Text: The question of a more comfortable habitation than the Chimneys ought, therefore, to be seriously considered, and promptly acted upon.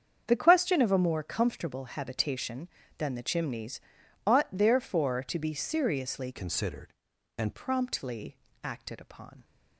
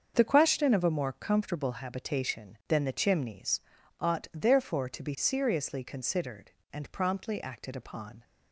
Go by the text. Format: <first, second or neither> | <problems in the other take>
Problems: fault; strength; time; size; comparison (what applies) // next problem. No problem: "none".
second | starts louder than the rest; strong; until 1.2 s; 7.5 dB; also in the second // pauses between "Chimneys" and "ought"; noticeable; at 3.7 s; 0.46 s long; also in the second // changes voice from "considered" to "and"; from 6.3 to 7.5 s; 1.2 s long // pauses between "promptly" and "acted"; slight; at 8.3 s; 0.30 s long